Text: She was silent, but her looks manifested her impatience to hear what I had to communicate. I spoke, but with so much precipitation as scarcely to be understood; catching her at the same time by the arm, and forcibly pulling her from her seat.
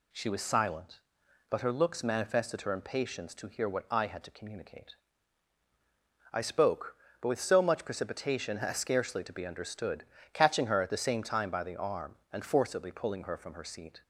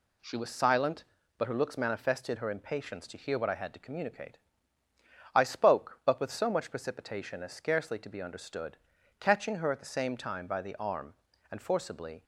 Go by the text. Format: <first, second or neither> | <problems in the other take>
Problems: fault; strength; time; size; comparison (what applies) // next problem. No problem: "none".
first | stops before "pulling her from her seat"; at 12.2 s